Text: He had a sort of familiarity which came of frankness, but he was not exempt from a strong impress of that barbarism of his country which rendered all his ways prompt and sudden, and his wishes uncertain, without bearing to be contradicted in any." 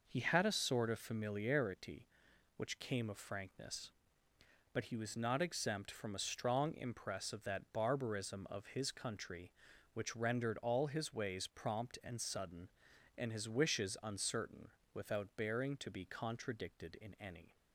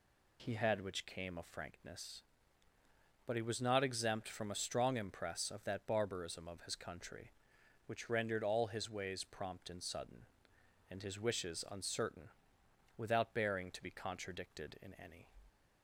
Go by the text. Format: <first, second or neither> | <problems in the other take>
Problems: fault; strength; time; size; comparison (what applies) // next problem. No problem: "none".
first | skips "a sort of familiarity"; at 0.8 s